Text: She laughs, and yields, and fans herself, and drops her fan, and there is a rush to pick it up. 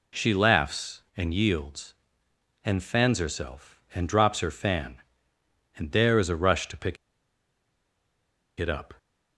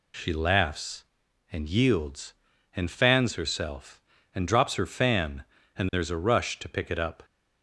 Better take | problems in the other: second | pauses between "pick" and "it"; strong; at 6.9 s; 1.6 s long

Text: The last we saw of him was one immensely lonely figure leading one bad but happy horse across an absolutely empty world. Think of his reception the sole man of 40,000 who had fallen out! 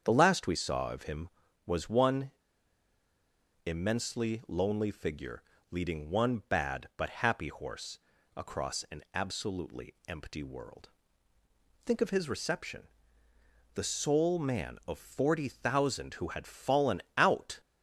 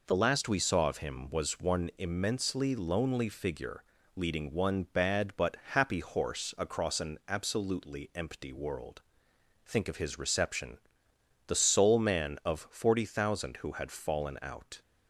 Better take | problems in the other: second | starts louder than the rest; strong; until 1.0 s; 7.5 dB // pauses between "one" and "immensely"; strong; at 2.3 s; 1.3 s long // pauses between "figure" and "leading"; slight; at 5.4 s; 0.28 s long; slight in the second // pauses between "horse" and "across"; at 7.9 s; 0.38 s long // pauses between "reception" and "the"; noticeable; at 12.8 s; 0.86 s long; noticeable in the second

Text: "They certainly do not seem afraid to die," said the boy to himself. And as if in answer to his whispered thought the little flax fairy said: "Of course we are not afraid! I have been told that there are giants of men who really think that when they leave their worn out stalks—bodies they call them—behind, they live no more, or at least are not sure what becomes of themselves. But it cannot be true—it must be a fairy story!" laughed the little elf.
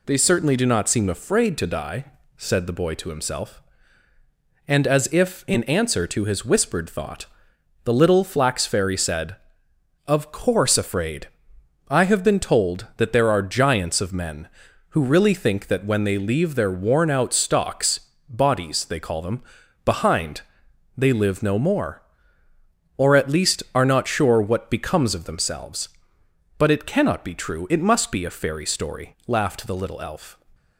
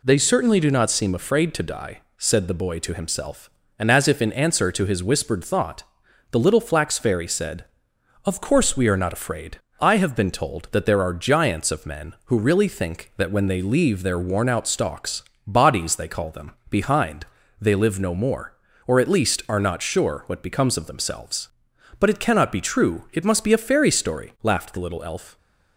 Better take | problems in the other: second | pauses between "thought" and "the"; noticeable; at 7.2 s; 0.58 s long; noticeable in the second // skips "we are not"; at 10.7 s

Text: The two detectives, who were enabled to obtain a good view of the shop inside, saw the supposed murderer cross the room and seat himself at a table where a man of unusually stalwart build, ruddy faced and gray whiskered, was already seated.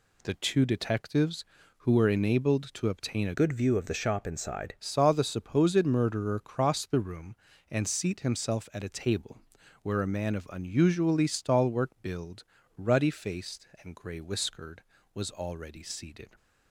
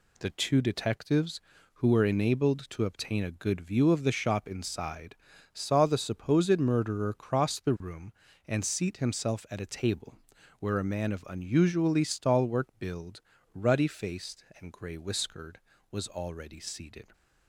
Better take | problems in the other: second | changes voice from "good" to "inside"; from 3.3 to 4.7 s; 1.4 s long // pauses between "table" and "where"; at 9.3 s; 0.44 s long; also in the second

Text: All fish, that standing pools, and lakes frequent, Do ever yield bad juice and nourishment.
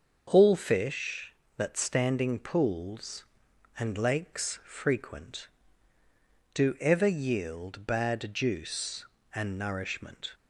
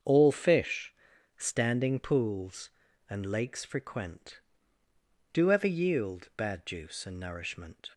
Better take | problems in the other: first | starts louder than the rest; until 1.4 s; 7 dB; also in the first // skips "that"; at 1.1 s

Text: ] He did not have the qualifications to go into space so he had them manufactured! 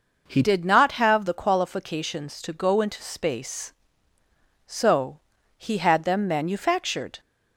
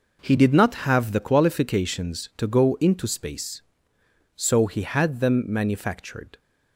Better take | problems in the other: second | changes voice at "did"; from 0.4 s on; 6.7 s long // pauses between "so" and "he"; slight; at 5.1 s; 0.36 s long

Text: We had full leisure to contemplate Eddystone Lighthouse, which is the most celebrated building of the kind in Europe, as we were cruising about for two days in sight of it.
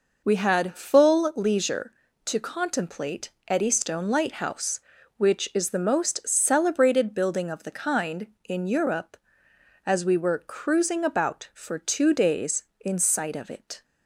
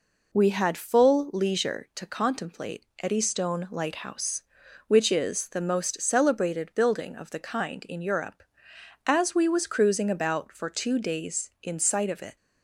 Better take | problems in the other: first | pauses between "contemplate" and "Eddystone"; slight; at 2.8 s; 0.16 s long; slight in the first // says "was" for "were"; at 9.4 s

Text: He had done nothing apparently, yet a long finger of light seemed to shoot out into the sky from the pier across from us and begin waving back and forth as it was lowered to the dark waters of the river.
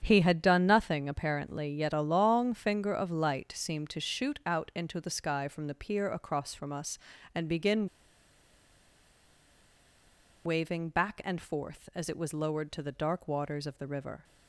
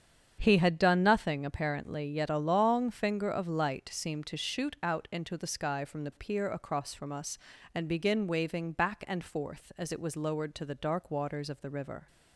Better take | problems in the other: second | starts louder than the rest; strong; until 1.0 s; 8 dB; strong in the second // pauses between "begin" and "waving"; strong; at 7.8 s; 2.5 s long

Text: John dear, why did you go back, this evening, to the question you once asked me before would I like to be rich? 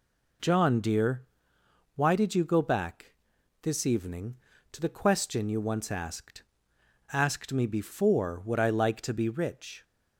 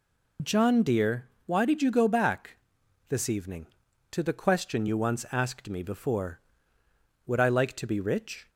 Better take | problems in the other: second | says "asked" twice; at 7.1 s

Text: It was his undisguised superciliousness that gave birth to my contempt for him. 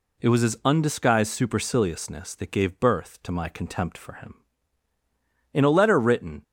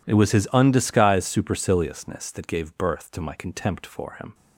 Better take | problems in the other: second | goes on to say "In a letter written"; noticeable; from 5.5 s on; 0.90 s long

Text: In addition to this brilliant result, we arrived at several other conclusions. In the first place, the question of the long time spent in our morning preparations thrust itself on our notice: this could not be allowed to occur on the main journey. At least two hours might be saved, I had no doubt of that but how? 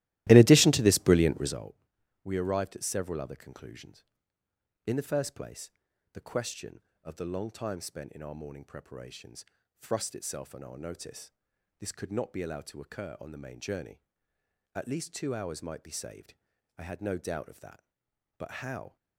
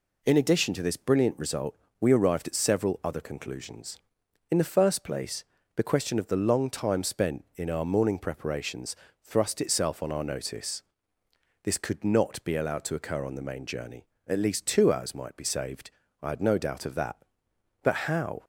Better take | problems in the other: second | starts louder than the rest; strong; until 1.6 s; 16 dB // pauses between "preparations" and "thrust"; slight; at 9.4 s; 0.34 s long; slight in the second

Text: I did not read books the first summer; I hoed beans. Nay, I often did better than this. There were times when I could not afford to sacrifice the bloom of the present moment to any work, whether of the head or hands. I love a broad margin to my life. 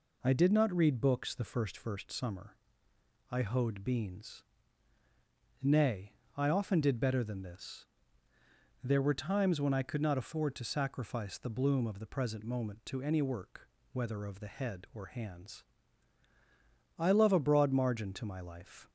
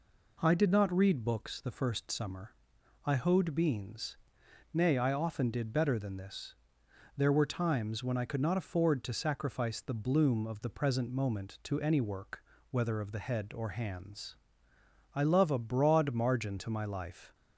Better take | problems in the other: second | says "first" twice; at 1.7 s

